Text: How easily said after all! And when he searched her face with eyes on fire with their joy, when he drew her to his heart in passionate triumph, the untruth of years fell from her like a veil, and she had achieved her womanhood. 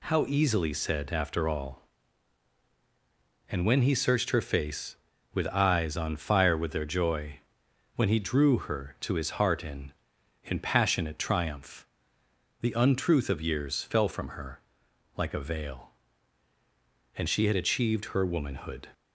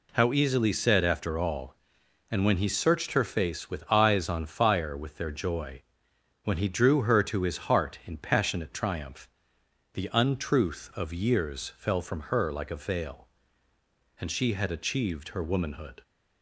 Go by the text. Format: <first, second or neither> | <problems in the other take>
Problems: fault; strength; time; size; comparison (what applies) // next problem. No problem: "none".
second | says "in" twice; at 10.4 s // pauses between "her" and "like"; noticeable; at 14.5 s; 0.56 s long